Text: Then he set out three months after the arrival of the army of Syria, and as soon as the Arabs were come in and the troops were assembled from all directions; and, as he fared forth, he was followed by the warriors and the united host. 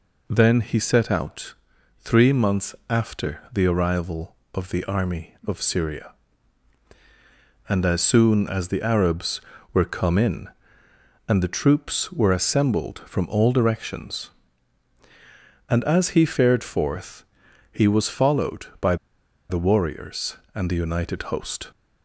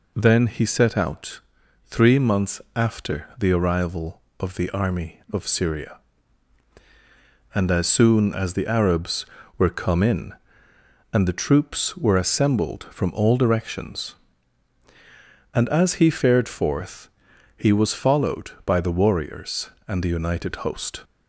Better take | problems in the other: second | pauses between "out" and "three"; noticeable; at 1.5 s; 0.46 s long; noticeable in the second // pauses between "by" and "the"; noticeable; at 18.9 s; 0.54 s long

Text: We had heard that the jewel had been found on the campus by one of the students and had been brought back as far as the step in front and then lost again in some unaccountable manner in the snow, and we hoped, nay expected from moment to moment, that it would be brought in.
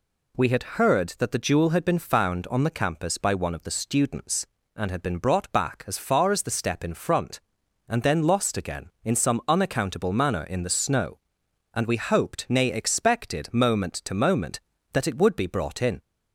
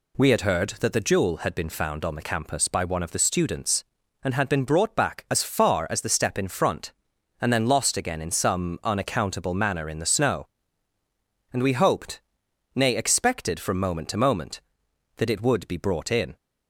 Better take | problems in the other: second | skips "from"; at 13.5 s

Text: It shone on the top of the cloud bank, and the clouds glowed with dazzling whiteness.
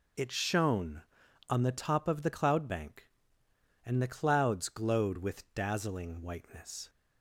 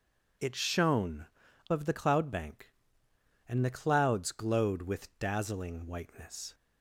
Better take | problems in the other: first | skips "on the top"; at 1.4 s

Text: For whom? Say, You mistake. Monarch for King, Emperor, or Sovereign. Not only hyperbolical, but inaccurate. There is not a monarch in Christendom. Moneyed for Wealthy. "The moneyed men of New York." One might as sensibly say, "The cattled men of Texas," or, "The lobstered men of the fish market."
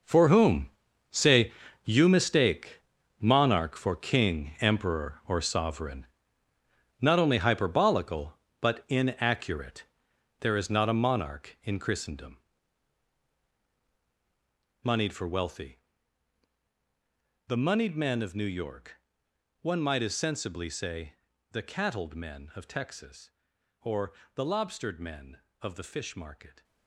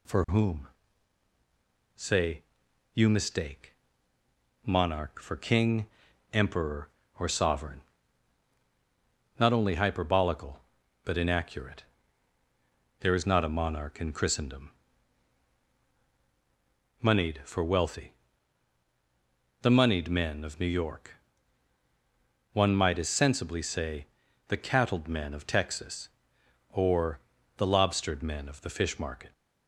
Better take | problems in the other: second | gets quieter; strong; throughout; 12.5 dB

